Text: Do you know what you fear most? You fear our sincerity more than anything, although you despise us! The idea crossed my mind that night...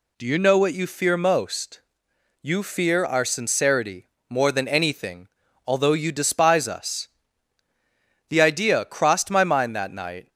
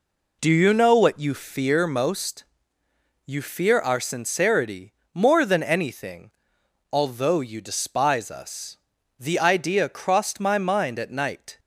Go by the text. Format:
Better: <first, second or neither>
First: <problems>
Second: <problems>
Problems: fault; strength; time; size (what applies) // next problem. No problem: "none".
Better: first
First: pauses between "sincerity" and "more"; slight; at 4.1 s; 0.20 s long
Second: pauses between "sincerity" and "more"; slight; at 4.9 s; 0.20 s long // says "at" for "that"; at 10.9 s